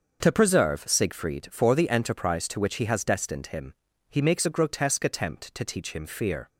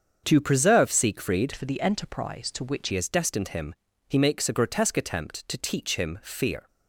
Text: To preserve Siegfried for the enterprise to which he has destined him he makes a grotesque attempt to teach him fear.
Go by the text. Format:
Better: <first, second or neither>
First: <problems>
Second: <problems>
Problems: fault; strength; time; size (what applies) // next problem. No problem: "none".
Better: first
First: starts louder than the rest; until 1.2 s; 6.5 dB // pauses between "him" and "he"; at 3.7 s; 0.38 s long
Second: starts louder than the rest; until 1.2 s; 7 dB // changes voice from "for" to "which"; from 1.5 to 2.8 s; 1.3 s long // pauses between "him" and "he"; slight; at 3.7 s; 0.34 s long